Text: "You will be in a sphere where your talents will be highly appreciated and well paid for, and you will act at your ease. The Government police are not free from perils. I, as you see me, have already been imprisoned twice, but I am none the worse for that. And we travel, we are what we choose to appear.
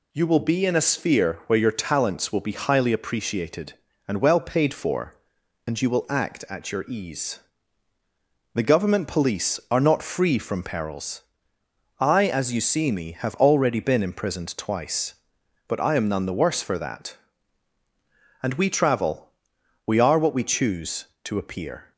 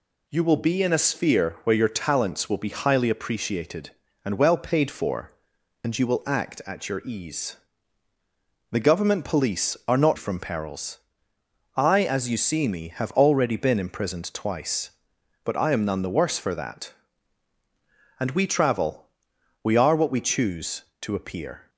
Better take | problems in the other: first | skips "free"; at 10.1 s

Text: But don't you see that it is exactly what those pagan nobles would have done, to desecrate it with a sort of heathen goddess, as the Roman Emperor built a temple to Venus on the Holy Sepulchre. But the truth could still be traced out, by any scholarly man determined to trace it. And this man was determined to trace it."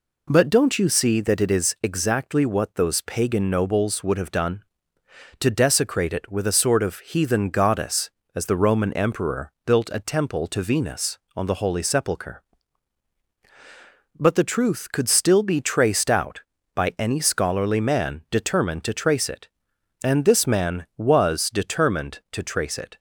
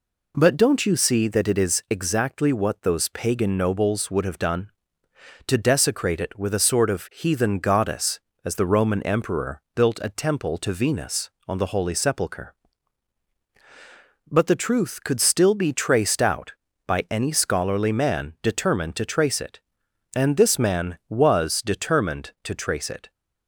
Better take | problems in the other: neither | none

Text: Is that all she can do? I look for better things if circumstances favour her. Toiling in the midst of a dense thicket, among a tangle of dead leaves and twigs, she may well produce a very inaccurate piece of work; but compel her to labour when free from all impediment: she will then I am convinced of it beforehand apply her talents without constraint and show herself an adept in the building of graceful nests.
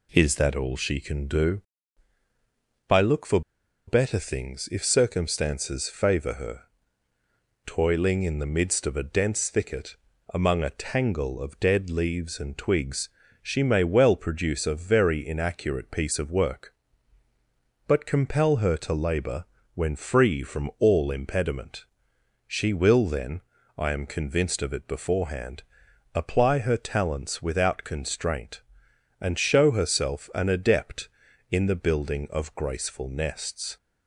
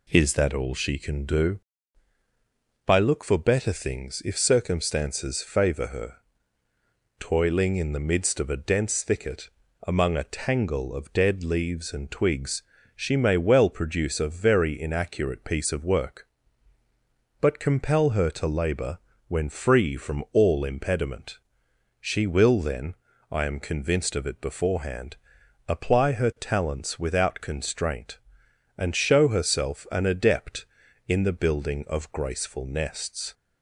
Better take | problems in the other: second | pauses between "for" and "better"; noticeable; at 3.3 s; 0.47 s long // pauses between "labour" and "when"; slight; at 19.4 s; 0.28 s long; slight in the second // pauses between "then" and "I"; slight; at 23.4 s; 0.36 s long; slight in the second // pauses between "beforehand" and "apply"; noticeable; at 25.6 s; 0.52 s long; noticeable in the second

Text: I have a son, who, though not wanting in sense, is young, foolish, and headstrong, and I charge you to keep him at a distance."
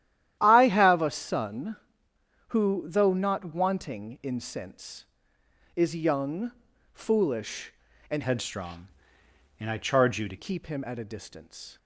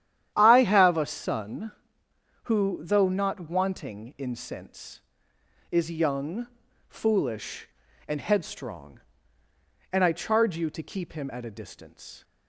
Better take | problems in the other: second | starts louder than the rest; strong; until 1.4 s; 11.5 dB; strong in the second // changes voice from "headstrong" to "to"; from 8.2 to 10.3 s; 2.1 s long

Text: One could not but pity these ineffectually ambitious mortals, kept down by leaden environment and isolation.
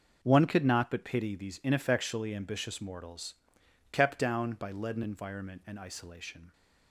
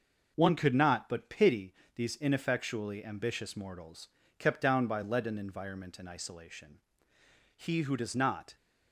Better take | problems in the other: first | pauses between "pity" and "these"; slight; at 1.7 s; 0.22 s long // goes on to say "He who does not"; noticeable; from 7.5 s on; 0.97 s long

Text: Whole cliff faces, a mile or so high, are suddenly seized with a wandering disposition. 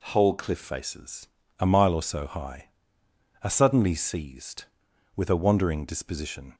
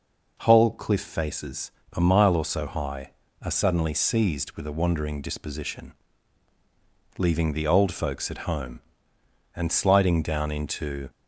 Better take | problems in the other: first | goes on to say "Leaving the old folks at home and sliding down into"; strong; from 7.1 s on; 3.9 s long

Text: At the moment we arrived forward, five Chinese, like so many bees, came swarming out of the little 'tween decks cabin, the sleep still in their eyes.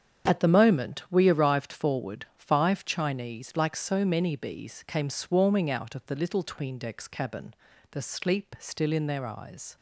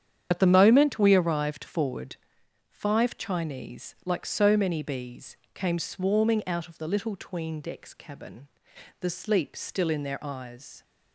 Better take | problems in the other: first | loses the start of "At"; at 0.3 s; 55 ms // starts louder than the rest; strong; until 1.3 s; 8.5 dB; strong in the first

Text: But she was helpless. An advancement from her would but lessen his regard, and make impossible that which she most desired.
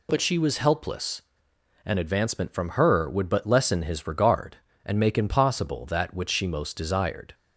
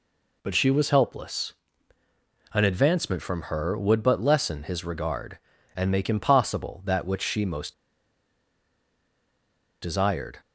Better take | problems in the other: first | pauses between "most" and "desired"; strong; at 7.7 s; 2.0 s long

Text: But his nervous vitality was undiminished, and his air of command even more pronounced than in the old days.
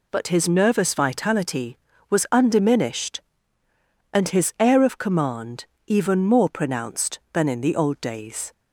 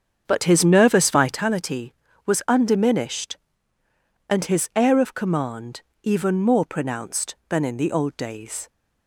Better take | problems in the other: first | starts louder than the rest; strong; until 1.4 s; 7.5 dB // pauses between "command" and "even"; slight; at 5.8 s; 0.20 s long; slight in the first

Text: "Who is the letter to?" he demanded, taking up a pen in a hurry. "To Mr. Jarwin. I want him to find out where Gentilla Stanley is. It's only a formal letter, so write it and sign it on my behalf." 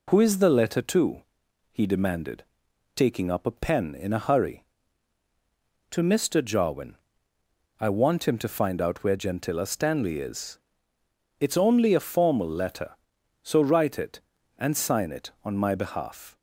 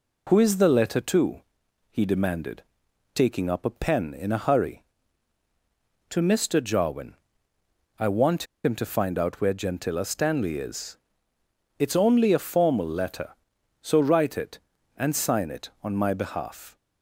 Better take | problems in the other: first | pauses between "want" and "him"; slight; at 8.4 s; 0.18 s long

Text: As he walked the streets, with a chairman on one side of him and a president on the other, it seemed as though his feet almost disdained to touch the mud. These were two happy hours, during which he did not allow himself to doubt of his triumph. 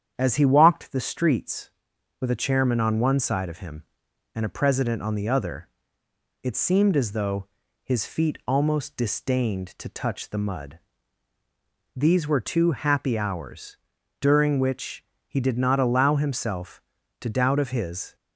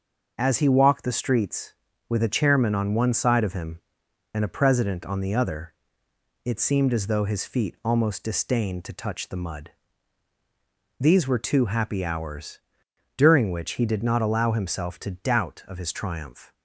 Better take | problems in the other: second | starts louder than the rest; strong; until 1.1 s; 8.5 dB; also in the second // pauses between "though" and "his"; slight; at 7.4 s; 0.36 s long // pauses between "which" and "he"; slight; at 15.0 s; 0.24 s long // stops before "triumph"; at 18.1 s

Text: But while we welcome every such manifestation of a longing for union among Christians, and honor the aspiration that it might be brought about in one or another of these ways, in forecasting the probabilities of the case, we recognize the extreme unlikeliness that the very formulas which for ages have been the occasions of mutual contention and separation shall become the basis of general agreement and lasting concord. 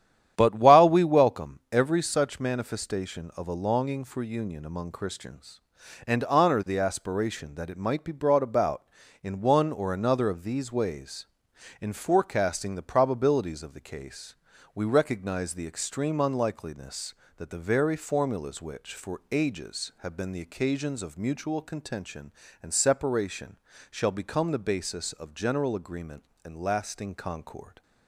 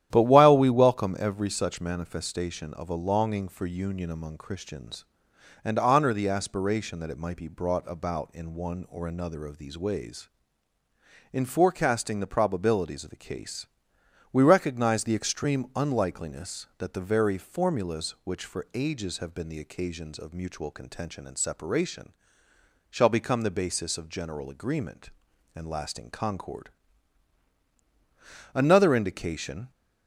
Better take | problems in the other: first | starts louder than the rest; strong; until 1.1 s; 11 dB; strong in the first // pauses between "separation" and "shall"; noticeable; at 22.1 s; 0.78 s long; slight in the first // goes on to say "Another indication"; noticeable; from 28.5 s on; 1.1 s long

